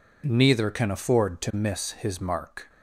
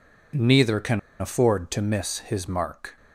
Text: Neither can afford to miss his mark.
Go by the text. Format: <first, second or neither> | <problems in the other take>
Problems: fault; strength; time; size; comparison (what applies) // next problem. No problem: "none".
first | pauses between "can" and "afford"; slight; at 0.9 s; 0.20 s long